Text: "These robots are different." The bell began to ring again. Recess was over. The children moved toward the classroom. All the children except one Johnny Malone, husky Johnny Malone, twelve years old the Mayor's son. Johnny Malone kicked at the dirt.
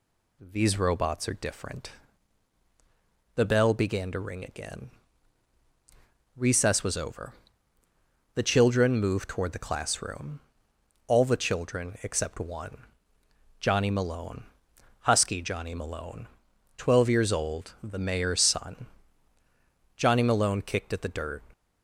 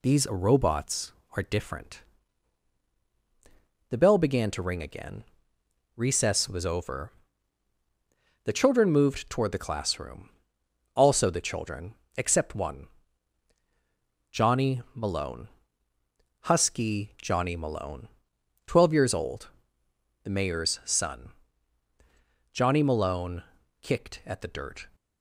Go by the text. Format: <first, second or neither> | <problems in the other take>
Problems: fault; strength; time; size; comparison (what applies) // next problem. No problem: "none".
first | says "Also" for "All"; at 10.9 s // pauses between "children" and "except"; slight; at 11.9 s; 0.22 s long // pauses between "one" and "Johnny"; strong; at 12.8 s; 1.4 s long; noticeable in the first // pauses between "old" and "the"; noticeable; at 19.4 s; 0.74 s long // pauses between "Malone" and "kicked"; at 23.4 s; 0.38 s long